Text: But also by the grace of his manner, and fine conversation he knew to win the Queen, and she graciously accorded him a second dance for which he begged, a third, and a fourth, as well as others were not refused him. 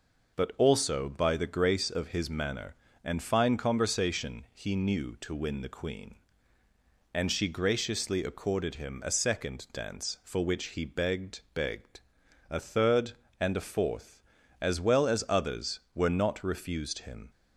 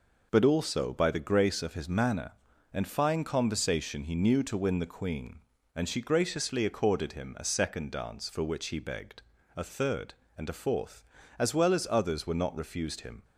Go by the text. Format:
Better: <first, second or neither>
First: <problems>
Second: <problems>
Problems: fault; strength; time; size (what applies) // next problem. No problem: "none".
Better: second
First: says "begged" twice; at 11.5 s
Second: none